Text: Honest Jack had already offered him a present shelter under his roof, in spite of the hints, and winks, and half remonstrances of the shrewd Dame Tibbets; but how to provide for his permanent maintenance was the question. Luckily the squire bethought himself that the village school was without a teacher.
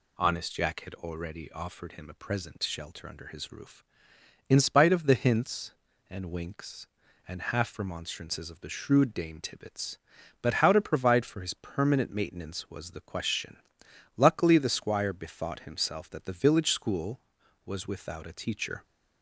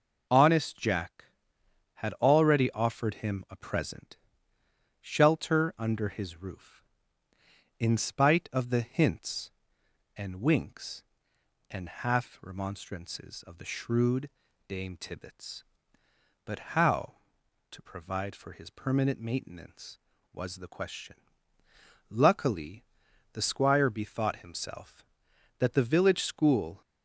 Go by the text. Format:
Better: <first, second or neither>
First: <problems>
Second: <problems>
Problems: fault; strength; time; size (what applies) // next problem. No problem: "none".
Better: first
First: none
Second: pauses between "present" and "shelter"; noticeable; at 4.1 s; 0.82 s long // pauses between "shrewd" and "Dame"; slight; at 14.3 s; 0.36 s long // pauses between "Luckily" and "the"; noticeable; at 22.8 s; 0.50 s long // stops before "was without a teacher"; at 26.8 s